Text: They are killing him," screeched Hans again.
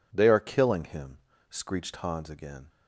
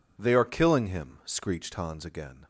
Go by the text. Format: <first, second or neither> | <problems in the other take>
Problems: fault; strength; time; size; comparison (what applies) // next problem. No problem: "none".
neither | none